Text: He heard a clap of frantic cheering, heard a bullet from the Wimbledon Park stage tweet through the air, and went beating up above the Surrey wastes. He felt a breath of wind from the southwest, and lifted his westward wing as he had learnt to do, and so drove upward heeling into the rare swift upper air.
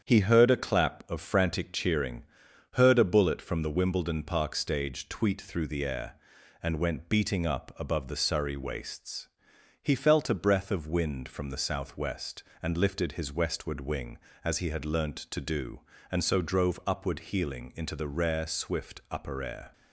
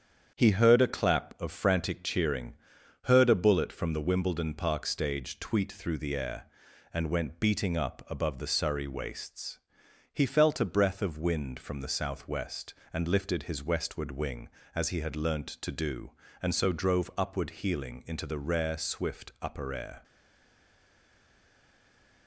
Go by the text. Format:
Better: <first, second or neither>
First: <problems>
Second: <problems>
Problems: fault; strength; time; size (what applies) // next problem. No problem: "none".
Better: first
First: starts louder than the rest; strong; until 1.0 s; 8 dB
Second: starts louder than the rest; strong; until 1.3 s; 8 dB // stays silent after the last word; from 20.0 s on; 2.2 s long